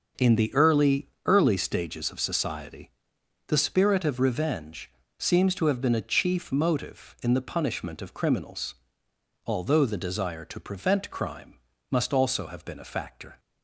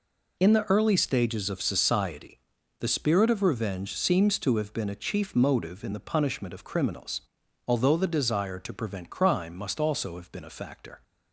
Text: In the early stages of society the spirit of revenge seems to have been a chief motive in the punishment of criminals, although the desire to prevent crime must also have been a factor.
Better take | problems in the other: second | says "early" twice; at 1.2 s // pauses between "society" and "the"; noticeable; at 2.9 s; 0.56 s long; also in the second // pauses between "revenge" and "seems"; slight; at 4.8 s; 0.28 s long // pauses between "crime" and "must"; slight; at 11.5 s; 0.34 s long

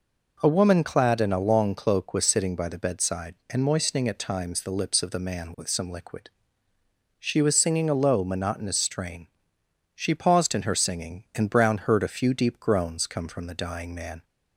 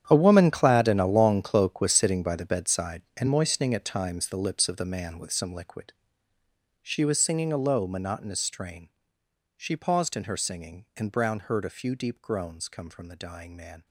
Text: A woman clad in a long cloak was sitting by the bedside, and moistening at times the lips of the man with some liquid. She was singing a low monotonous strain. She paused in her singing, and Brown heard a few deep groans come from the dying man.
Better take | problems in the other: first | gets quieter; strong; throughout; 16.5 dB

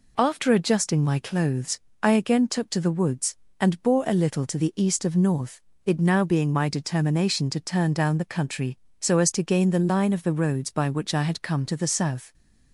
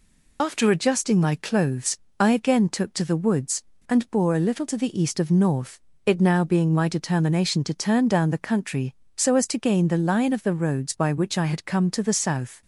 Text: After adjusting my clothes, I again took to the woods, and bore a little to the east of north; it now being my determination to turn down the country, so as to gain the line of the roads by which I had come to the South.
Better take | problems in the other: first | loses the start of "After"; at 0.3 s; 65 ms

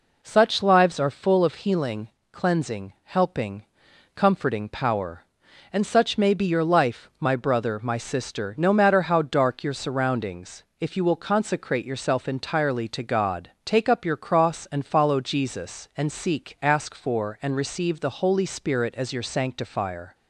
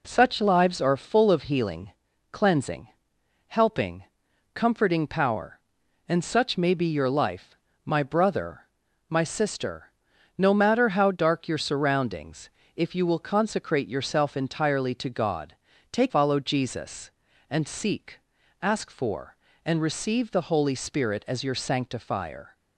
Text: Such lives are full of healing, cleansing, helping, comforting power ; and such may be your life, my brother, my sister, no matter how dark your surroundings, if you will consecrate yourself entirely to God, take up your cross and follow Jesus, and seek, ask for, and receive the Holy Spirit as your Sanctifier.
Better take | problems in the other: first | skips "up your cross and"; at 16.1 s

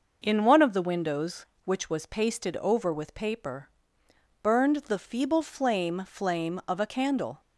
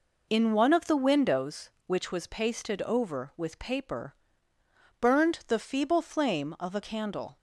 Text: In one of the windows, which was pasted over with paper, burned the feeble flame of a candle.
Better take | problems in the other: second | says "flame" twice; at 6.0 s

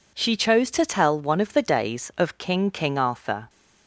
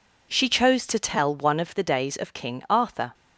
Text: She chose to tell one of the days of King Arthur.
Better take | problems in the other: second | says "King" twice; at 2.6 s

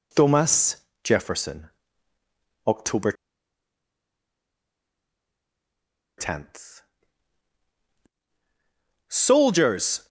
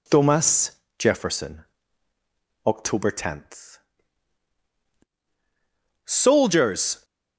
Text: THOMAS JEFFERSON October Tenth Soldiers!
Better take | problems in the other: second | pauses between "THOMAS" and "JEFFERSON"; slight; at 0.7 s; 0.30 s long; slight in the second // pauses between "JEFFERSON" and "October"; noticeable; at 1.6 s; 0.98 s long; also in the second // pauses between "October" and "Tenth"; strong; at 3.1 s; 3.0 s long // pauses between "Tenth" and "Soldiers"; strong; at 6.8 s; 2.2 s long; strong in the second

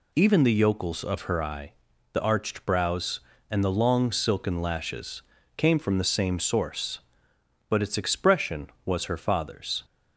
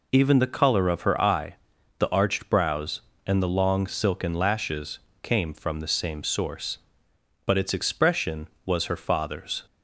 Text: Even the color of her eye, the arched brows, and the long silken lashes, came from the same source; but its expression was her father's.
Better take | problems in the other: second | says "yokels" for "color"; at 0.5 s

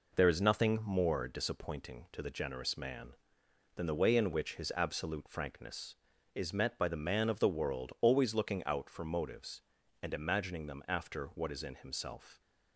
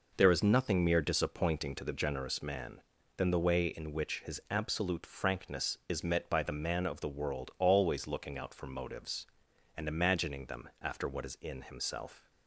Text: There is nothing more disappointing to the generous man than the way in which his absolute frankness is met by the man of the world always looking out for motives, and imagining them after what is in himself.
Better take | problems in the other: first | says "mere" for "more"; at 0.8 s

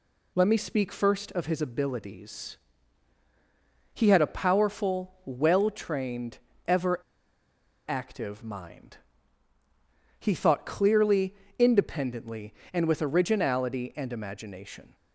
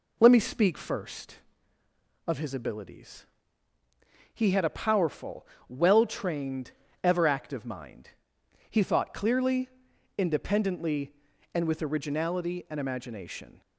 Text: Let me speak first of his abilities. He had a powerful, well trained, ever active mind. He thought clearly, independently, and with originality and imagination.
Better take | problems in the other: second | pauses between "ever" and "active"; noticeable; at 6.9 s; 0.87 s long

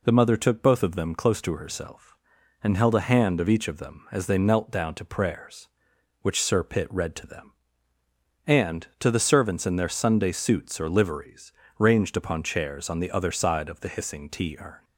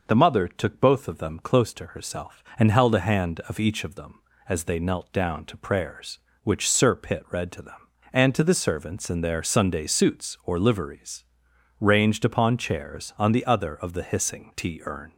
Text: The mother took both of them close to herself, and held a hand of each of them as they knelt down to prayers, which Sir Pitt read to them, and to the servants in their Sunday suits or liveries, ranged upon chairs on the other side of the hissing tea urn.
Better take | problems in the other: first | skips "side"; at 13.7 s

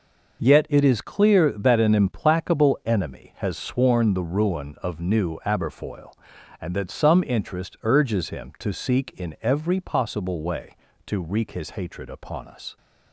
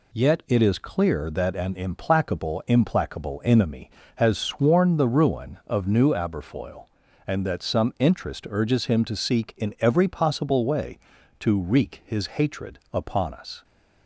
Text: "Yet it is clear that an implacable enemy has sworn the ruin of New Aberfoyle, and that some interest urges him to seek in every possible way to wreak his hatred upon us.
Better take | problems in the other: first | says "implacable" twice; at 2.6 s

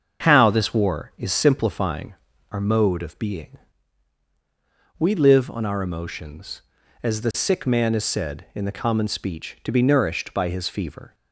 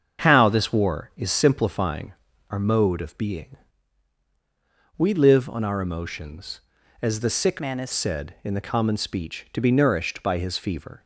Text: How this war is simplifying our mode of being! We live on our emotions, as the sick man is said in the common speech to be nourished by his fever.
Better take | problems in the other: first | starts louder than the rest; until 1.2 s; 7 dB; also in the first // pauses between "simplifying" and "our"; at 2.1 s; 0.38 s long; also in the first // changes voice from "man" to "is"; from 7.5 to 7.9 s; 0.4 s long

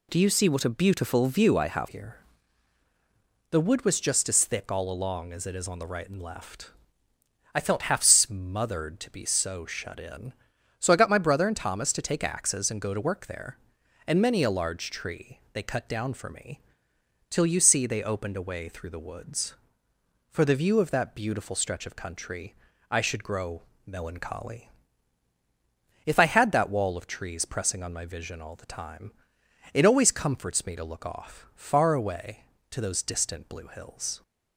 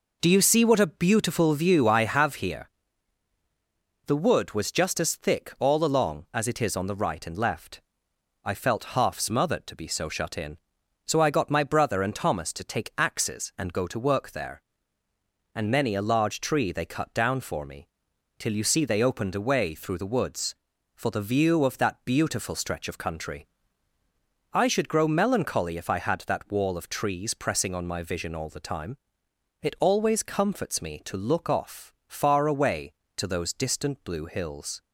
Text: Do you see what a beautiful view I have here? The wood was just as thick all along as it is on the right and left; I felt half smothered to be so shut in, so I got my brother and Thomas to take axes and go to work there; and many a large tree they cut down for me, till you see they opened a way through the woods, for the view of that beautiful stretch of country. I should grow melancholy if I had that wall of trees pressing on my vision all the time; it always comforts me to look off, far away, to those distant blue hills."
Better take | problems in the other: second | changes voice at "here"; from 1.8 s on; 32.4 s long // pauses between "grow" and "melancholy"; slight; at 23.6 s; 0.22 s long // pauses between "melancholy" and "if"; strong; at 24.6 s; 1.3 s long

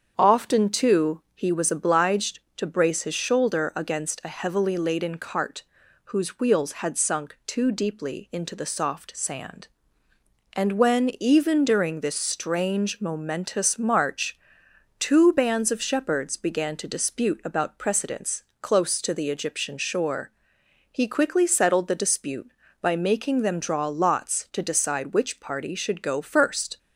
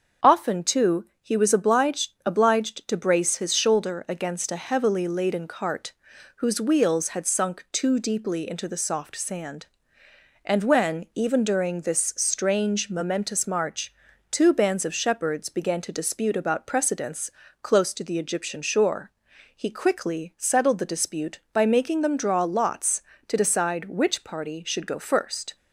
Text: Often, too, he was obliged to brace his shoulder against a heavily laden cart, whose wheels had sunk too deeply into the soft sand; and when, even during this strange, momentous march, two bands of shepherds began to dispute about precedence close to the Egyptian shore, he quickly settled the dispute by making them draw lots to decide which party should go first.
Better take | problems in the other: first | starts louder than the rest; until 1.3 s; 6.5 dB; strong in the first // says "obliged" twice; at 2.2 s // pauses between "precedence" and "close"; slight; at 17.2 s; 0.32 s long; slight in the first

